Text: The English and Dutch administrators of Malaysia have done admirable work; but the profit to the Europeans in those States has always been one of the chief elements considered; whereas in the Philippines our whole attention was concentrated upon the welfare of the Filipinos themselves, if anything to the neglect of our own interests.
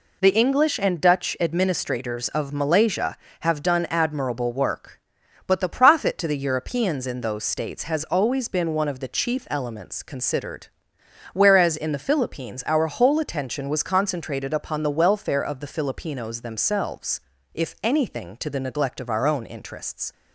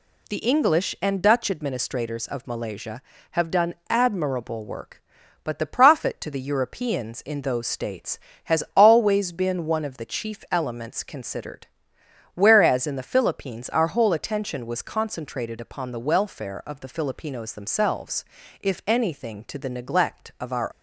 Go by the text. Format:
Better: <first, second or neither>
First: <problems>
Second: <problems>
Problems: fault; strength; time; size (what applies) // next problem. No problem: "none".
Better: first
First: none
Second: stops before "own interests"; at 20.7 s